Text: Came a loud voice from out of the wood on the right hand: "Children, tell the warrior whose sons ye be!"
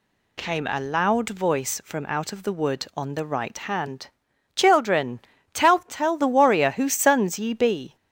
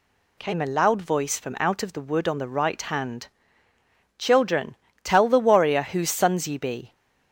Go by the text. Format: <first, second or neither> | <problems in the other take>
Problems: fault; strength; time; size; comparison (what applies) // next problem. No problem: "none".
second | says "tell" twice; at 5.7 s